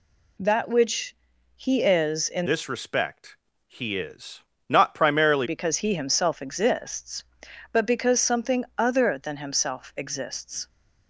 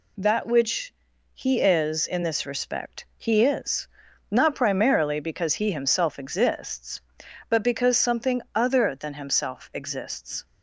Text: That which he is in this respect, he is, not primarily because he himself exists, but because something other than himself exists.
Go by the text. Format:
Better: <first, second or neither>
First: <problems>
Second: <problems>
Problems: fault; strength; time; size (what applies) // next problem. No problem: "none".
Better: second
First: pauses between "which" and "he"; at 1.1 s; 0.40 s long // changes voice from "this" to "primarily"; from 2.4 to 5.4 s; 3.0 s long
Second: pauses between "which" and "he"; at 0.9 s; 0.40 s long